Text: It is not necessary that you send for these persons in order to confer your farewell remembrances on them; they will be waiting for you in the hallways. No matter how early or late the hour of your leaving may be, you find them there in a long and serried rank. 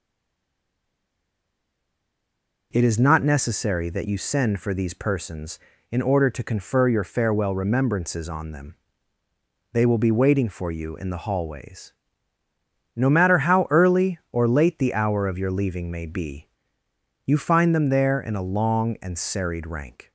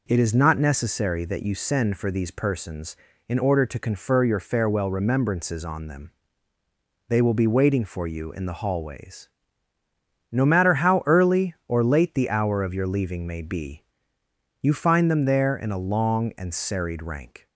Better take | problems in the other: second | stays silent before the first word; strong; until 2.7 s; 2.7 s long

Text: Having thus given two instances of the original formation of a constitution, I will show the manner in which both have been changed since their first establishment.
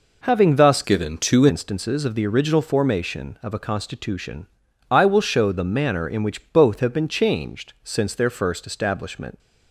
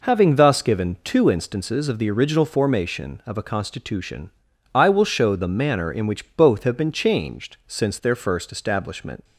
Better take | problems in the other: second | changes voice from "given" to "two"; from 0.8 to 1.4 s; 0.6 s long

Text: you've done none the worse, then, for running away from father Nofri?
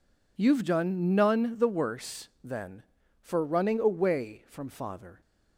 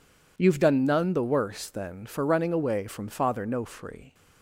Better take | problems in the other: second | stops before "Nofri"; at 5.2 s

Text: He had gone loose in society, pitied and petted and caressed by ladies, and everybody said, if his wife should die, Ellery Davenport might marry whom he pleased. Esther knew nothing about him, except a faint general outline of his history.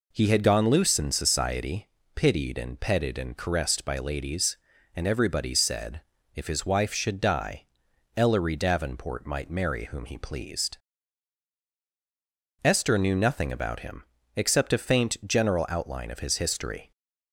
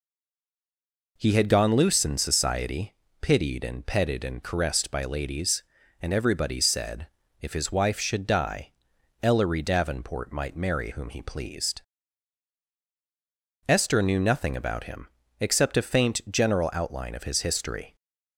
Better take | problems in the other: first | stays silent before the first word; noticeable; until 1.1 s; 1.1 s long

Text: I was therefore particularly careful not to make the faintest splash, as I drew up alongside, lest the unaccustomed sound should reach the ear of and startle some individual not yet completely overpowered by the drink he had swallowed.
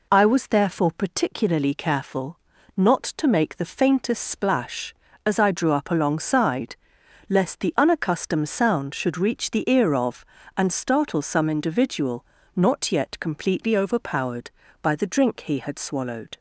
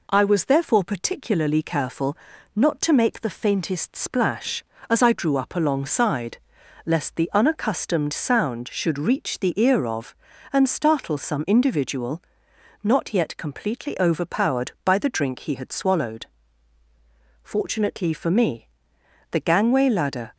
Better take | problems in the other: first | pauses between "careful" and "not"; at 2.1 s; 0.40 s long; also in the first // pauses between "individual" and "not"; noticeable; at 12.2 s; 0.62 s long; slight in the first // goes on to say "Fortunately for me the gangway ladder"; strong; from 17.4 s on; 2.9 s long

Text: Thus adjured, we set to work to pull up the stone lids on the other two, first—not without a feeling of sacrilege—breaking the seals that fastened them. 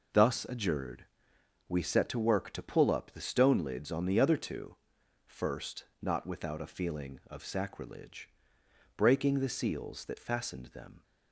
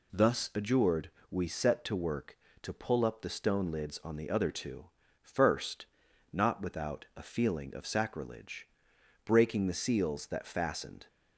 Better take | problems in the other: first | stops before "them"; at 11.0 s

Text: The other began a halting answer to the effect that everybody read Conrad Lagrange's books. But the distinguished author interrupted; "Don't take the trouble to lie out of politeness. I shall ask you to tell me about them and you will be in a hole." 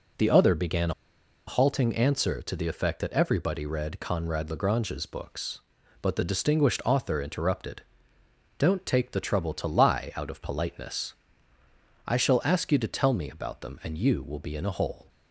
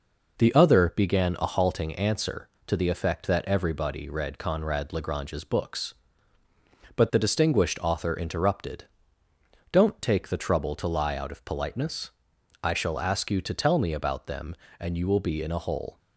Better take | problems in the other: second | pauses between "began" and "a"; noticeable; at 0.9 s; 0.56 s long

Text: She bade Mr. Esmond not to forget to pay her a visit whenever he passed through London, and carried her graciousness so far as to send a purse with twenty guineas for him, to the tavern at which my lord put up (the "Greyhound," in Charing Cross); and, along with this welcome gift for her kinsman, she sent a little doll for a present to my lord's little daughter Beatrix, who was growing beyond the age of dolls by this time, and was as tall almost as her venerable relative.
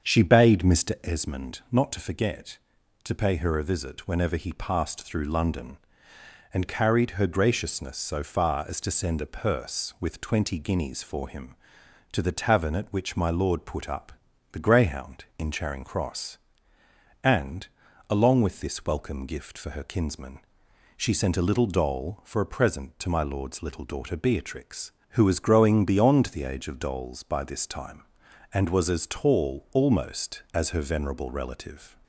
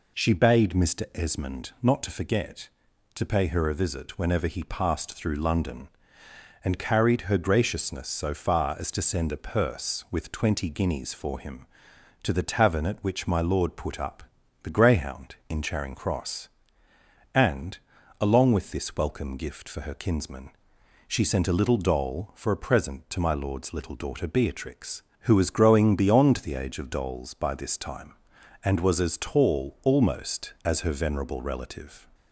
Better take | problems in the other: second | starts louder than the rest; strong; until 1.1 s; 7.5 dB

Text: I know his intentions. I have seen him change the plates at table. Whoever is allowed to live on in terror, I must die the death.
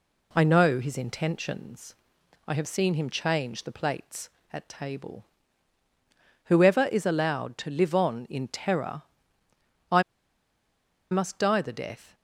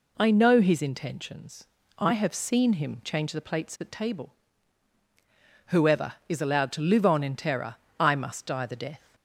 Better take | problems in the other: second | pauses between "I" and "must"; at 10.0 s; 1.0 s long

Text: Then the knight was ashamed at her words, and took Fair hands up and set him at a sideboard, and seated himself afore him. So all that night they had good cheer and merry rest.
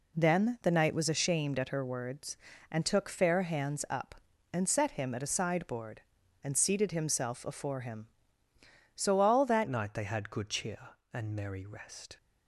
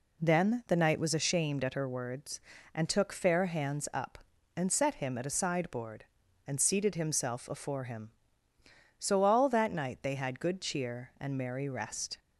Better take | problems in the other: second | changes voice at "night"; from 9.6 s on; 2.5 s long

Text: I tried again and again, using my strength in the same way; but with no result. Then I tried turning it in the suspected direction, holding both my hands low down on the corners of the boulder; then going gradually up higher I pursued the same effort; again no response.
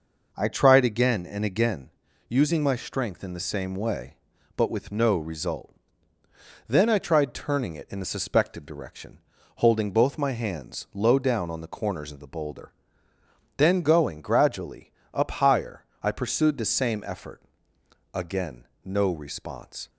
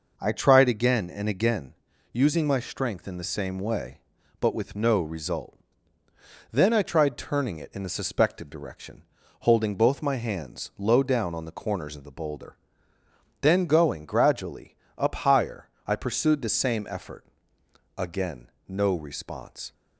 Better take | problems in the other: neither | pauses between "gradually" and "up"; slight; the same in both // pauses between "higher" and "I"; slight; the same in both // pauses between "again" and "no"; slight; the same in both

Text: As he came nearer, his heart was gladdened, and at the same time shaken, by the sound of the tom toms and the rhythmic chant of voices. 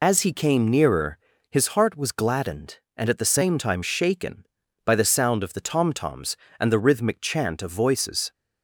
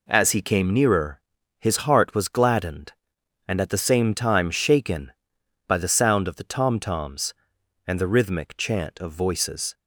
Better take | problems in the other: second | loses the start of "As"; at 0.0 s; 55 ms

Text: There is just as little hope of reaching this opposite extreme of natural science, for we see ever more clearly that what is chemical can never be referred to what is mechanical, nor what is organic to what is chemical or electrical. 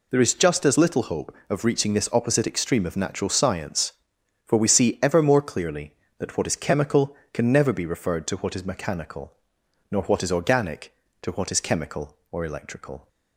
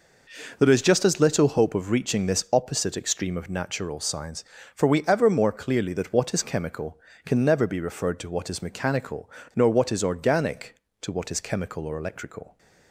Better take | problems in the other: first | skips "see"; at 5.0 s

